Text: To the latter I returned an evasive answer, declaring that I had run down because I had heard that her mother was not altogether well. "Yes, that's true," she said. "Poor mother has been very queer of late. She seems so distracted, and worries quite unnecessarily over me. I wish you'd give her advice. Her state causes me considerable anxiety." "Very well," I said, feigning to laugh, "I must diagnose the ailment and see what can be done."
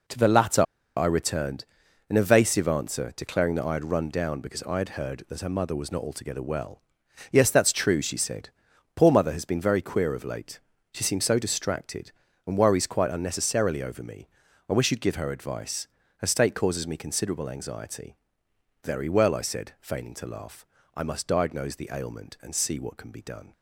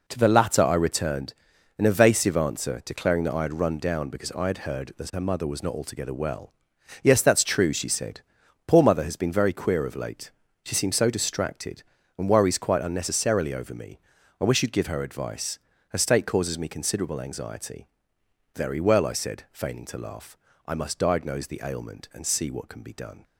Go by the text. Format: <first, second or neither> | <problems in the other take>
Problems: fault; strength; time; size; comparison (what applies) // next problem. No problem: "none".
second | pauses between "latter" and "I"; slight; at 0.6 s; 0.34 s long // pauses between "returned" and "an"; noticeable; at 1.6 s; 0.46 s long; noticeable in the second